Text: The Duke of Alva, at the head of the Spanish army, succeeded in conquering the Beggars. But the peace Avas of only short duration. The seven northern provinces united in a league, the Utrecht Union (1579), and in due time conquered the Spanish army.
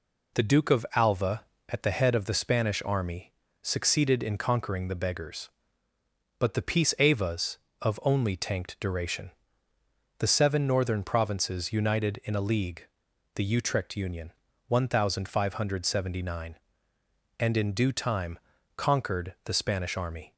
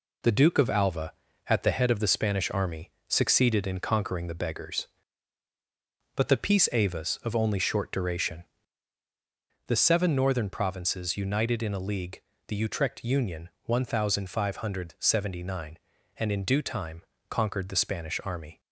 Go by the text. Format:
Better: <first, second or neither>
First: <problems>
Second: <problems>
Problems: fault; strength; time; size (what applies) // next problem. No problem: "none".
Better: second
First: says "tanked" for "short"; at 8.3 s // pauses between "time" and "conquered"; slight; at 18.3 s; 0.36 s long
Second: pauses between "time" and "conquered"; slight; at 17.0 s; 0.26 s long